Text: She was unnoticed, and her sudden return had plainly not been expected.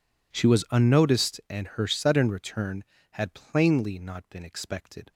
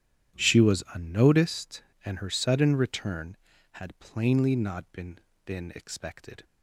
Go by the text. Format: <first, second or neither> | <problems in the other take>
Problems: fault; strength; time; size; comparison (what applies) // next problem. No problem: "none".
first | says "been" twice; at 5.4 s